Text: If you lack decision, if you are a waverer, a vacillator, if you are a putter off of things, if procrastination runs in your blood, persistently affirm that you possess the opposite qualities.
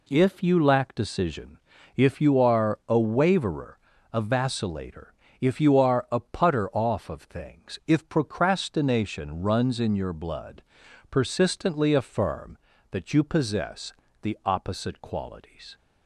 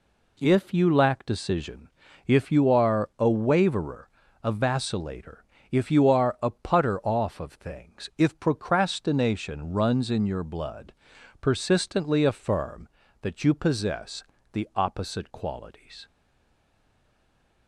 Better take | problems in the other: first | pauses between "possess" and "the"; slight; at 14.2 s; 0.28 s long; slight in the first // stays silent after the last word; noticeable; from 16.0 s on; 1.6 s long

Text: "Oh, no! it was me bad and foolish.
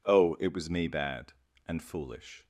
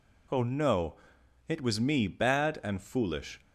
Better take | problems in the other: second | skips "no"; at 0.3 s

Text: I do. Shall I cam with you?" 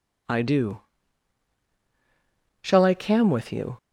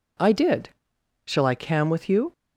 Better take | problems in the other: first | says "did" for "do"; at 0.3 s

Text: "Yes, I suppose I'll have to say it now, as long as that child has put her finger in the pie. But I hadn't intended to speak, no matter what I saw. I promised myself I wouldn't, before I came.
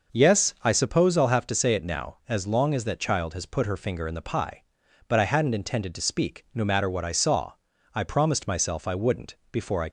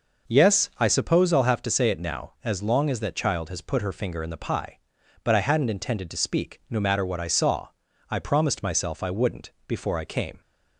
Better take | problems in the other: second | stops before "came"; at 9.8 s

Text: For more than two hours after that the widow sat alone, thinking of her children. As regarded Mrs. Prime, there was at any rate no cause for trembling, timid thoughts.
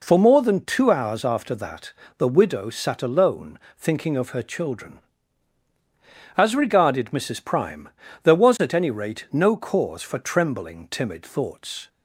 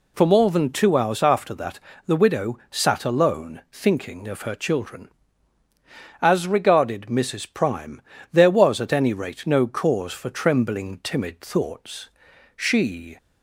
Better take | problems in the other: first | pauses between "that" and "the"; slight; at 1.8 s; 0.26 s long; slight in the first // goes on to say "She"; noticeable; from 12.5 s on; 0.62 s long

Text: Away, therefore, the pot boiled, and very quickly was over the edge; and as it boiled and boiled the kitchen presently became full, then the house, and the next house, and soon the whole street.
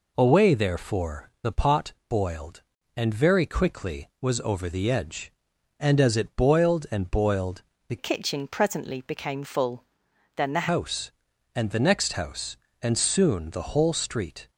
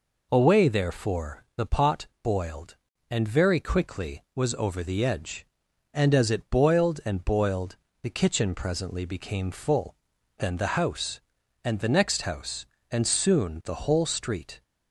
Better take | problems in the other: second | pauses between "boiled" and "the"; slight; at 7.6 s; 0.26 s long; slight in the second // changes voice from "kitchen" to "the"; from 7.9 to 10.6 s; 2.7 s long

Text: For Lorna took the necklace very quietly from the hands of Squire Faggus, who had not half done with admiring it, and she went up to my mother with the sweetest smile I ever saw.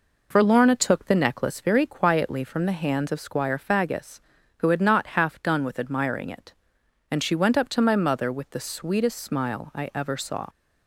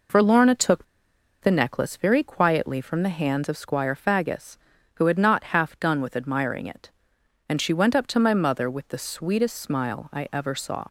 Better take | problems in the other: first | pauses between "took" and "the"; noticeable; at 0.8 s; 0.58 s long

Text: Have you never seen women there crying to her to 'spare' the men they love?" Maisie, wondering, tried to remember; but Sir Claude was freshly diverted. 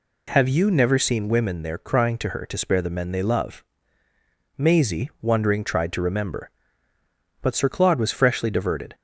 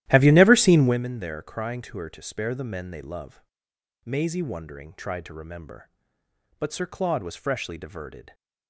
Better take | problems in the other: first | starts louder than the rest; strong; until 1.0 s; 13.5 dB

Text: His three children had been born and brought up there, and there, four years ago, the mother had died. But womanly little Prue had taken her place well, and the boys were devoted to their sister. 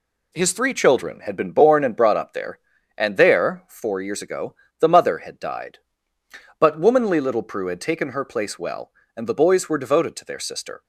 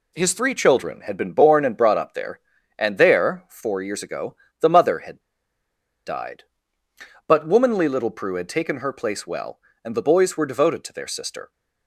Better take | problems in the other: first | pauses between "had" and "died"; noticeable; at 5.2 s; 0.85 s long

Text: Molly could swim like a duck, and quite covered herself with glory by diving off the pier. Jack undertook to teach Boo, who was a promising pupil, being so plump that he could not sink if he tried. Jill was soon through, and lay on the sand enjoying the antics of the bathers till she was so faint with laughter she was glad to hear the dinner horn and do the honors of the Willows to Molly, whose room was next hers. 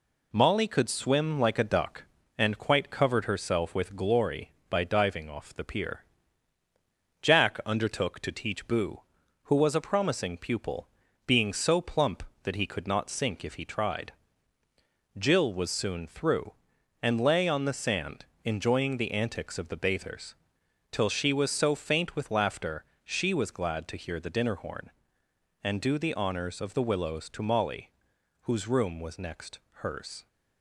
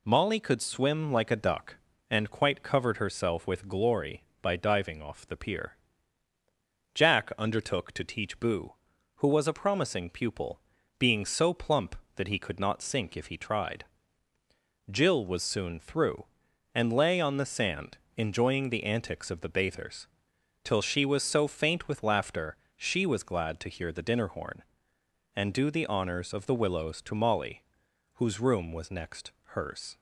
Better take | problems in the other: second | gets quieter; slight; throughout; 3 dB // pauses between "sand" and "enjoying"; slight; at 18.2 s; 0.18 s long; slight in the second // pauses between "bathers" and "till"; noticeable; at 20.3 s; 0.58 s long; noticeable in the second // pauses between "laughter" and "she"; slight; at 22.8 s; 0.18 s long; slight in the second // pauses between "next" and "hers"; slight; at 29.5 s; 0.22 s long; slight in the second

